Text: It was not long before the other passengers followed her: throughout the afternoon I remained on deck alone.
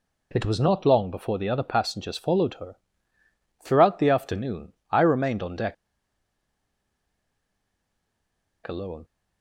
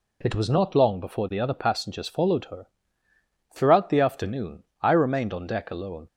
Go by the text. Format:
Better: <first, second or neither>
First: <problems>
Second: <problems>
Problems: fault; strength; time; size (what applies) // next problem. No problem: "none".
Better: second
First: pauses between "afternoon" and "I"; slight; at 4.7 s; 0.18 s long // pauses between "deck" and "alone"; strong; at 5.7 s; 2.9 s long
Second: pauses between "afternoon" and "I"; slight; at 4.6 s; 0.18 s long